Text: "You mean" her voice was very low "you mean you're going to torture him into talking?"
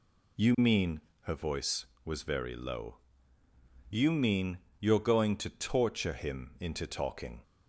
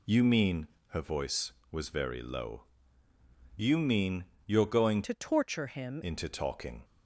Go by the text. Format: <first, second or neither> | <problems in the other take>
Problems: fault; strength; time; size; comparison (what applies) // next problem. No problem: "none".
first | pauses between "mean" and "her"; slight; at 0.6 s; 0.22 s long; slight in the first // pauses between "low" and "you"; noticeable; at 2.6 s; 0.92 s long; noticeable in the first // pauses between "mean" and "you're"; slight; at 4.2 s; 0.22 s long; slight in the first // changes voice from "to" to "him"; from 5.0 to 6.0 s; 1.0 s long